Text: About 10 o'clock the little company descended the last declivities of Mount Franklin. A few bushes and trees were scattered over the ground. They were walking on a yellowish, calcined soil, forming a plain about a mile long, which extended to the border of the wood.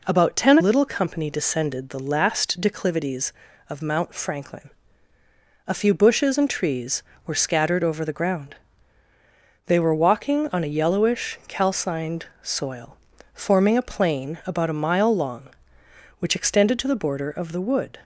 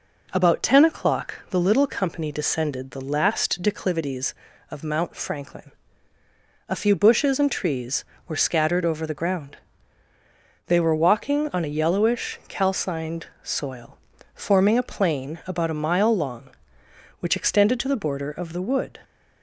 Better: second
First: skips "o'clock the"; at 0.5 s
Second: none

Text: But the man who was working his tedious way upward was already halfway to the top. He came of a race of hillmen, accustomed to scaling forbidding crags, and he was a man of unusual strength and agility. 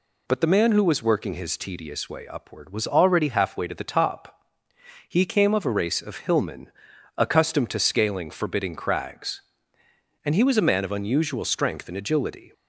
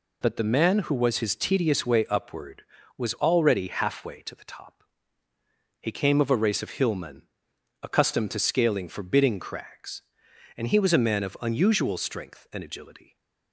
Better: first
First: none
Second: skips "working"; at 1.1 s

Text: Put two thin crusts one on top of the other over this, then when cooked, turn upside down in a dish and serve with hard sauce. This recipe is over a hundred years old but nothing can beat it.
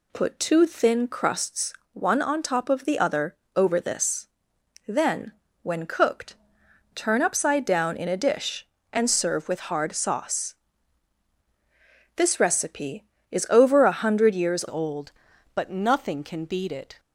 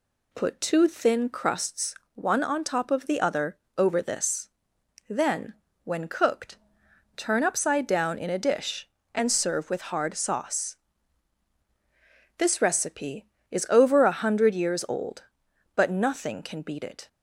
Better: second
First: pauses between "crusts" and "one"; slight; at 1.7 s; 0.20 s long // pauses between "other" and "over"; slight; at 3.3 s; 0.20 s long // pauses between "then" and "when"; slight; at 5.3 s; 0.30 s long // changes voice at "old"; from 14.6 s on; 2.3 s long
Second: pauses between "crusts" and "one"; slight; at 1.9 s; 0.20 s long // pauses between "other" and "over"; slight; at 3.5 s; 0.20 s long // pauses between "then" and "when"; slight; at 5.5 s; 0.30 s long

